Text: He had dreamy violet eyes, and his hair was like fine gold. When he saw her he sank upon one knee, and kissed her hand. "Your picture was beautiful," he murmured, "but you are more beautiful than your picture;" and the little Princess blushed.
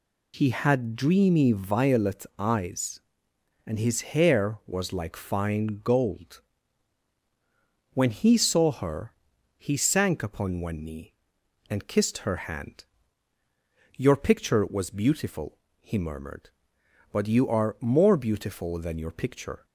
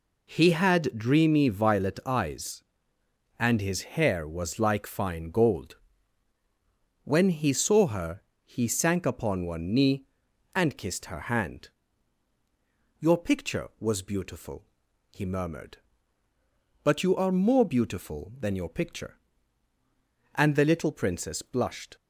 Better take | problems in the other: second | pauses between "her" and "he"; at 9.1 s; 0.44 s long; slight in the second // pauses between "her" and "hand"; slight; at 12.3 s; 0.16 s long // stops before "and the little Princess blushed"; at 19.6 s

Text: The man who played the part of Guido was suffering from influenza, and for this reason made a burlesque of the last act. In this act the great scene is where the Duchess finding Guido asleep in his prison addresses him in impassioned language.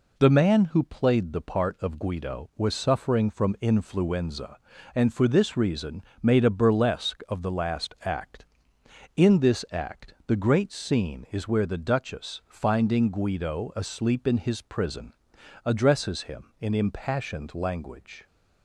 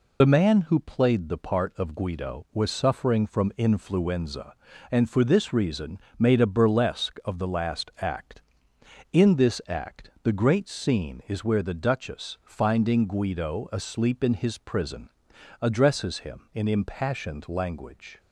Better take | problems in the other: first | loses the start of "The"; at 0.2 s; 55 ms // pauses between "reason" and "made"; slight; at 5.9 s; 0.20 s long; slight in the first // pauses between "prison" and "addresses"; noticeable; at 15.0 s; 0.54 s long; noticeable in the first

